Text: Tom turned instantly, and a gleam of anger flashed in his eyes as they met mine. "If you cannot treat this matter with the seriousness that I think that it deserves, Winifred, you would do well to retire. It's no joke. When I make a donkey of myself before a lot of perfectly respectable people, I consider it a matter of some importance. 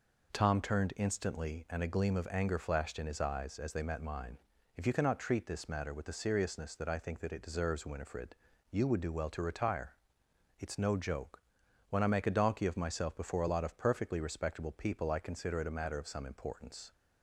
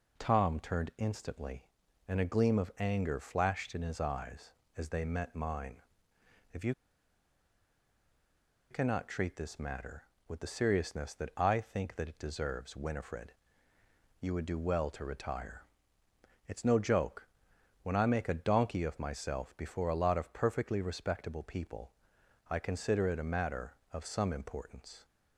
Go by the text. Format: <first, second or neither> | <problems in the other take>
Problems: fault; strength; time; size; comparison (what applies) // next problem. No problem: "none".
first | pauses between "you" and "cannot"; strong; at 6.7 s; 1.9 s long